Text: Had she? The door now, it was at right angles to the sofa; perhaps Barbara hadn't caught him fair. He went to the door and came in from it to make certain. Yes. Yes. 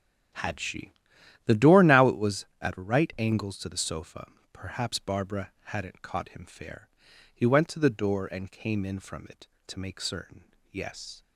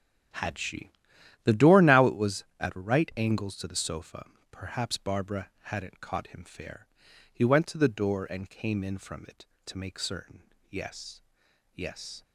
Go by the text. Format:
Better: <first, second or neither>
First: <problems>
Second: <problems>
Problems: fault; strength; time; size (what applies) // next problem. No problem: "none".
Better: second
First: starts louder than the rest; strong; until 1.8 s; 8.5 dB // stops before "Yes"; at 11.2 s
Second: starts louder than the rest; strong; until 1.8 s; 9 dB